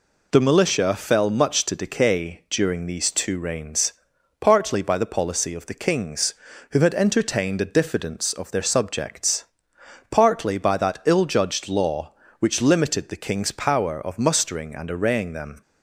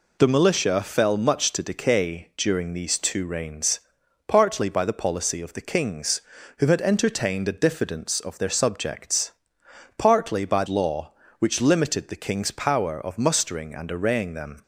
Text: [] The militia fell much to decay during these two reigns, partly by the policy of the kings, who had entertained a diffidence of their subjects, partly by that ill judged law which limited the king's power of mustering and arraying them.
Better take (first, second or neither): first